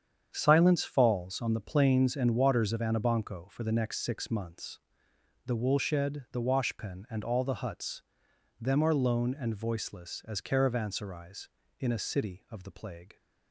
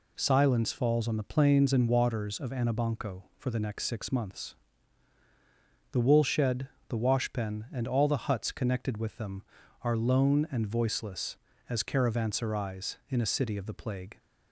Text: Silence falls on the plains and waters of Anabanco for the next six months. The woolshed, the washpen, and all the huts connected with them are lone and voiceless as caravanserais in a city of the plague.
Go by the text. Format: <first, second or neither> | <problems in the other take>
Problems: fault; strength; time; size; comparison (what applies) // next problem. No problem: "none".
second | starts louder than the rest; strong; until 1.3 s; 8 dB // skips "connected with"; at 8.2 s